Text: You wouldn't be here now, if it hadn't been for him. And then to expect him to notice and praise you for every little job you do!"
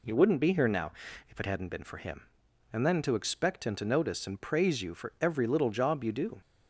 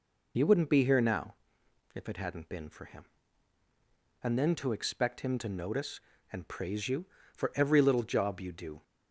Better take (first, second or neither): first